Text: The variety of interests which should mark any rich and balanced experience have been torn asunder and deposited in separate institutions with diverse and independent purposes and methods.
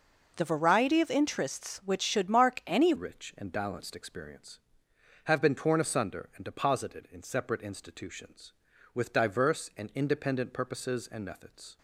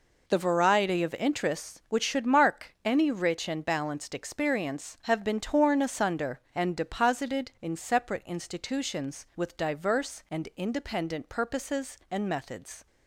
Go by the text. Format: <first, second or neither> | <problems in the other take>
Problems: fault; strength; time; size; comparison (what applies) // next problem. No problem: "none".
second | changes voice at "rich"; from 2.9 s on; 8.8 s long